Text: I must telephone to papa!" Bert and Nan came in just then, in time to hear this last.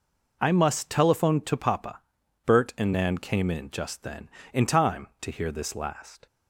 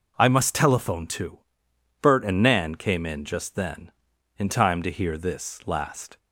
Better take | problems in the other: first | skips "papa"; at 1.6 s

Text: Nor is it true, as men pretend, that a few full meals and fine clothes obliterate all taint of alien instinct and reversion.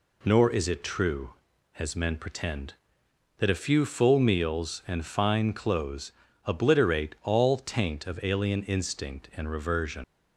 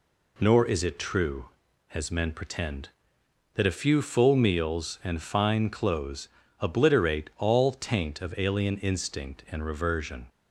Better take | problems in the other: second | pauses between "clothes" and "obliterate"; slight; at 6.1 s; 0.32 s long; slight in the second // leaves "reversion" unfinished; at 10.0 s; 95 ms

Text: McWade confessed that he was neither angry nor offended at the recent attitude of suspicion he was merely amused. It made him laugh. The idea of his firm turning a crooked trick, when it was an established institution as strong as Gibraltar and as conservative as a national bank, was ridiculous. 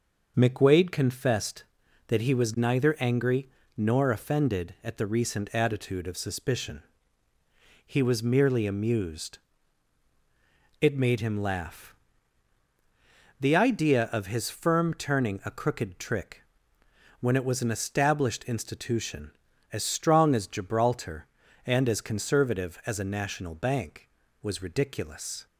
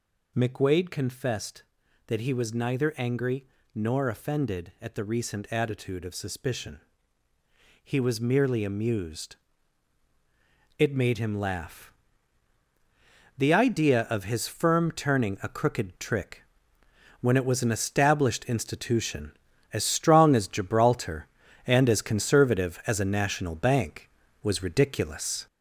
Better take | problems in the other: first | gets louder; noticeable; throughout; 4 dB // pauses between "angry" and "nor"; slight; at 3.4 s; 0.30 s long; slight in the first // pauses between "suspicion" and "he"; at 6.7 s; 1.0 s long; also in the first

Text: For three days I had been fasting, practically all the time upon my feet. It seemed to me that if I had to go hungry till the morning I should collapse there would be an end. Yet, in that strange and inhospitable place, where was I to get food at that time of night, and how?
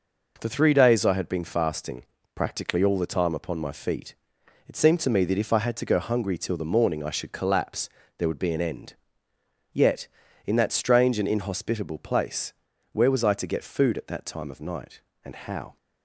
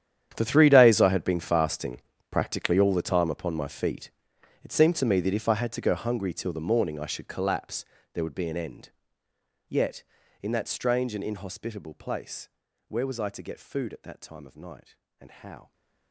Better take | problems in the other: first | gets quieter; strong; throughout; 18 dB // pauses between "collapse" and "there"; slight; at 7.8 s; 0.30 s long; slight in the first

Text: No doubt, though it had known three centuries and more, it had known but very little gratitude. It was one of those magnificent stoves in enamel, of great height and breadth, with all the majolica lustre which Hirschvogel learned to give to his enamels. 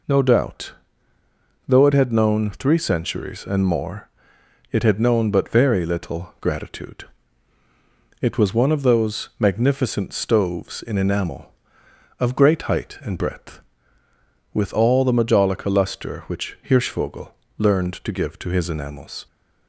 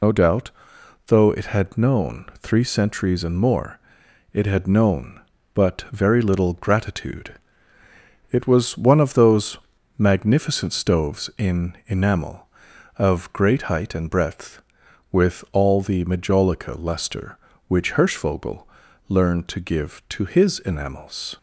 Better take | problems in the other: first | loses the start of "No"; at 0.0 s; 65 ms // pauses between "those" and "magnificent"; at 9.5 s; 0.40 s long // pauses between "Hirschvogel" and "learned"; at 18.6 s; 0.42 s long; slight in the first

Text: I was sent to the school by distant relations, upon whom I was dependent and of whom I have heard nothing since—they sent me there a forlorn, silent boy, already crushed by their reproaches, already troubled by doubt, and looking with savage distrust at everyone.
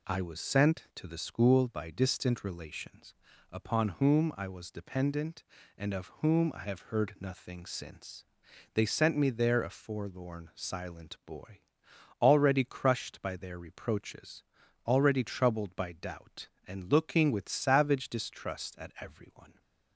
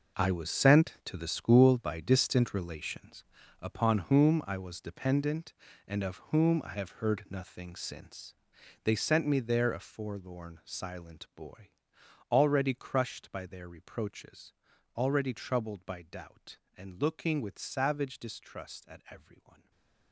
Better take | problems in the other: first | gets quieter; strong; throughout; 14 dB // stays silent after the last word; slight; from 19.5 s on; 0.6 s long

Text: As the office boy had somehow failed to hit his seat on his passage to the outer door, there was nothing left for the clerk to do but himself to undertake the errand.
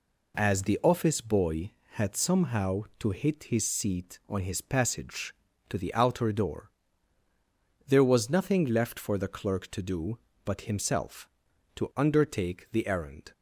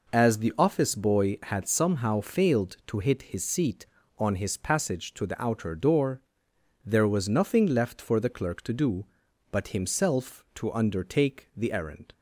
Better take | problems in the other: second | skips "failed"; at 2.9 s

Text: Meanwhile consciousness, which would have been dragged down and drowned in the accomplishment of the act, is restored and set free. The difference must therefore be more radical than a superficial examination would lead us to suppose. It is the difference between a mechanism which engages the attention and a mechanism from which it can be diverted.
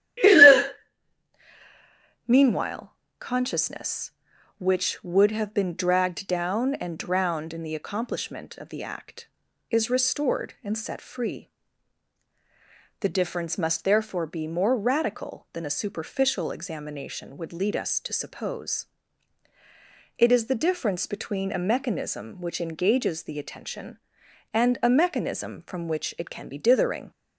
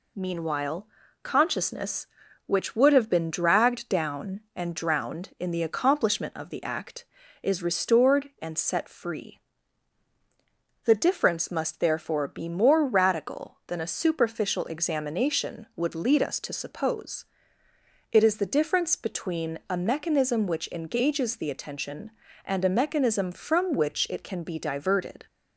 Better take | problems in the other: second | pauses between "Meanwhile" and "consciousness"; slight; at 2.9 s; 0.26 s long; slight in the second // says "dithering" for "diverted"; at 26.5 s

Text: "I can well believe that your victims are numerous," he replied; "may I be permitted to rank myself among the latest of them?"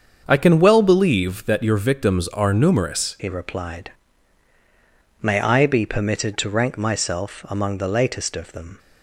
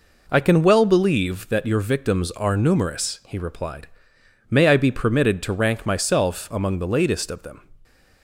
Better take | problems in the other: second | starts louder than the rest; until 1.2 s; 7 dB // changes voice at "he"; from 3.1 s on; 5.6 s long

